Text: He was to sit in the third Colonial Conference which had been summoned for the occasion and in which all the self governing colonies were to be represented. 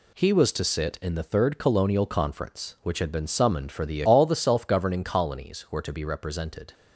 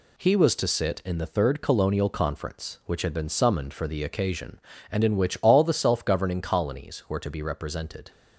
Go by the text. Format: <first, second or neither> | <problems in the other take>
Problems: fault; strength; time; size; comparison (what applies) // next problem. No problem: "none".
second | skips "occasion and in which"; at 4.0 s